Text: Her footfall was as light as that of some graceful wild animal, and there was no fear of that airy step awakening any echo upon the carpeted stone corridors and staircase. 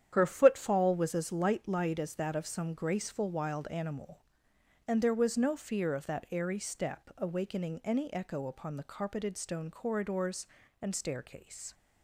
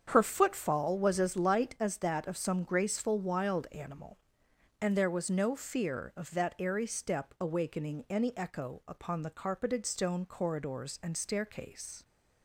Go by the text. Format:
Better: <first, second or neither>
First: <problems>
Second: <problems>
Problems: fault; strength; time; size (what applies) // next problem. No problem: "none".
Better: second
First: starts louder than the rest; strong; until 1.1 s; 9.5 dB // says "light" twice; at 1.6 s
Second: starts louder than the rest; strong; until 1.0 s; 7.5 dB